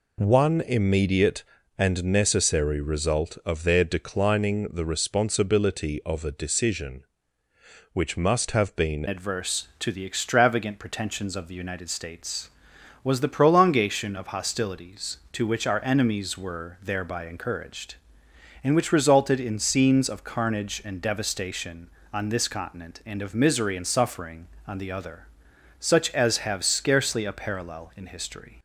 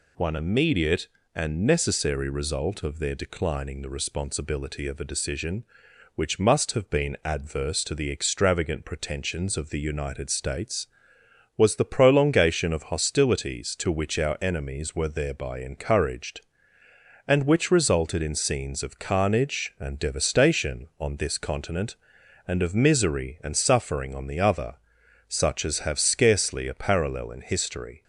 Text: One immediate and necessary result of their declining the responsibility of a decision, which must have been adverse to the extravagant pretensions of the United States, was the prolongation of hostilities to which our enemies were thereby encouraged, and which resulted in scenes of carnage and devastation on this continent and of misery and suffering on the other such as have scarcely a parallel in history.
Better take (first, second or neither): second